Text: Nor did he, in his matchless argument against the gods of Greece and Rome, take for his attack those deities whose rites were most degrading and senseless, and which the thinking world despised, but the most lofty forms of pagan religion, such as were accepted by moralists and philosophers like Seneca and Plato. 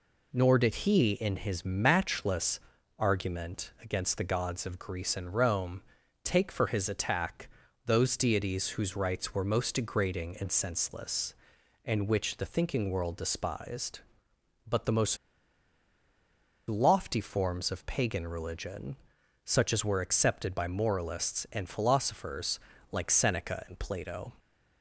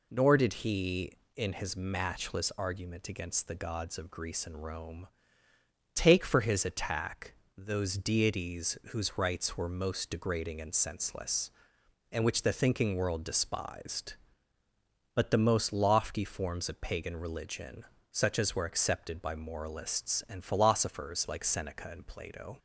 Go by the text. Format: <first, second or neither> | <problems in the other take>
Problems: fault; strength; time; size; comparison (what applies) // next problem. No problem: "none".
second | pauses between "matchless" and "argument"; at 2.5 s; 0.38 s long // pauses between "attack" and "those"; at 7.4 s; 0.38 s long; slight in the second // pauses between "most" and "lofty"; strong; at 15.1 s; 1.5 s long // pauses between "philosophers" and "like"; slight; at 22.5 s; 0.32 s long